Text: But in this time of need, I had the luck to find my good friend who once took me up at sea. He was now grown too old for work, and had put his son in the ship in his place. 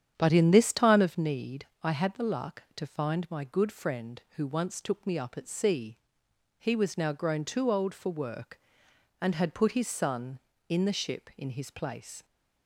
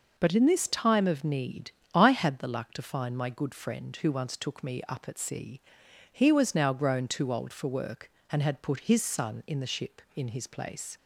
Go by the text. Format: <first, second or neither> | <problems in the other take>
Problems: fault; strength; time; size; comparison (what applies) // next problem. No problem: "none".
second | starts louder than the rest; strong; until 1.3 s; 9 dB